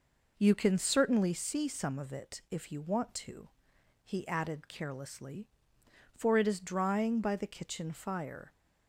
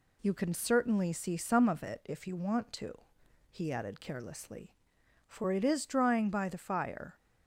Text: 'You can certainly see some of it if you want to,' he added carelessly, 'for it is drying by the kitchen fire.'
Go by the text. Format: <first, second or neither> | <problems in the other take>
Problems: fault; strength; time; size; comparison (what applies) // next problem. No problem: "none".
first | skips "kitchen"; at 6.5 s